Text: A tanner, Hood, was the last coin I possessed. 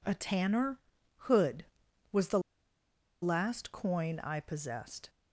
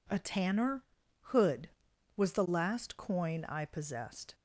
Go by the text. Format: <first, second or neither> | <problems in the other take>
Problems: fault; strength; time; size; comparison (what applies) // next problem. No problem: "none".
second | pauses between "the" and "last"; noticeable; at 2.3 s; 0.83 s long